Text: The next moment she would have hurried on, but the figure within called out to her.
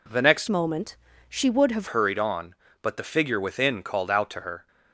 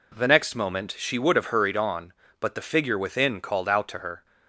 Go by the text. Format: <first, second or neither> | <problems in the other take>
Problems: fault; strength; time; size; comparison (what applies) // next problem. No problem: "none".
second | changes voice from "moment" to "have"; from 0.4 to 1.8 s; 1.4 s long // pauses between "moment" and "she"; slight; at 0.9 s; 0.32 s long